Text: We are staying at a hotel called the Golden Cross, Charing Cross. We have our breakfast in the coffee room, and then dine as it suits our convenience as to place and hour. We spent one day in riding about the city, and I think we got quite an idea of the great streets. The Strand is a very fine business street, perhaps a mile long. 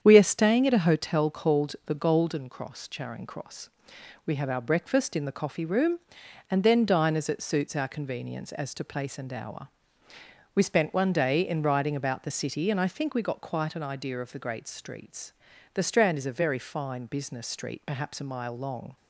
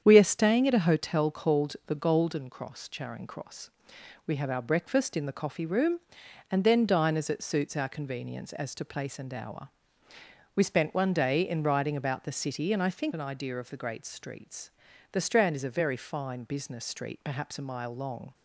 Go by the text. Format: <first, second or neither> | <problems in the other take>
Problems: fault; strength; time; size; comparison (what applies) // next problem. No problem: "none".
first | starts louder than the rest; strong; until 1.0 s; 8 dB; strong in the first // skips "we got quite"; at 13.1 s